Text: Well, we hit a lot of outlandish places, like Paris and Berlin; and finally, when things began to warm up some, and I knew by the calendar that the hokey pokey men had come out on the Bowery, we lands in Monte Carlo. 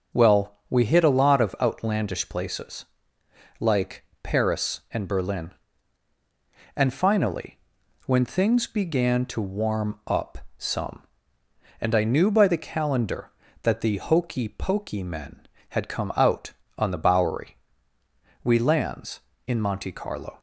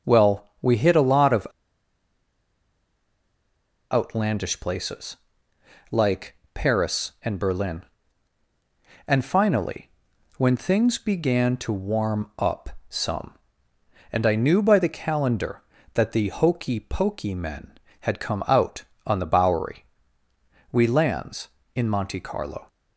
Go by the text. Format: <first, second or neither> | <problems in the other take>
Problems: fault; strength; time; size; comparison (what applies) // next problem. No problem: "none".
first | pauses between "of" and "outlandish"; strong; at 1.4 s; 2.4 s long // pauses between "like" and "Paris"; slight; at 6.3 s; 0.18 s long; slight in the first // pauses between "up" and "some"; slight; at 12.6 s; 0.22 s long; slight in the first